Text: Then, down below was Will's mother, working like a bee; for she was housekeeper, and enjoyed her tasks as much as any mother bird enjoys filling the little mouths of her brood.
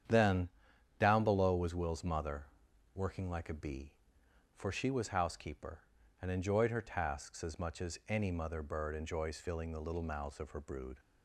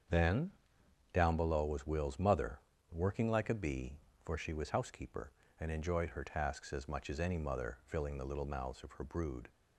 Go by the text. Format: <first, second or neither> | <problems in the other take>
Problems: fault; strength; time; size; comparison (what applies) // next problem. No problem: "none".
first | starts louder than the rest; strong; until 1.7 s; 7.5 dB; strong in the first // skips "bird enjoys"; at 7.8 s